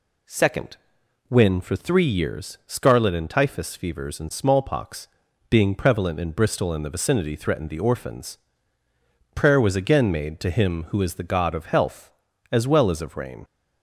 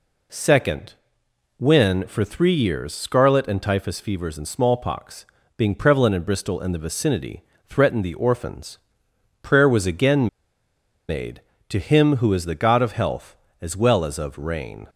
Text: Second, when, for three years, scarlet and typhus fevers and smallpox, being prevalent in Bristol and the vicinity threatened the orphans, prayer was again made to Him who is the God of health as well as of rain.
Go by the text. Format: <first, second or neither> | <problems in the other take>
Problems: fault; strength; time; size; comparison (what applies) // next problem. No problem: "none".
first | pauses between "vicinity" and "threatened"; slight; at 7.4 s; 0.24 s long // pauses between "again" and "made"; noticeable; at 10.2 s; 0.79 s long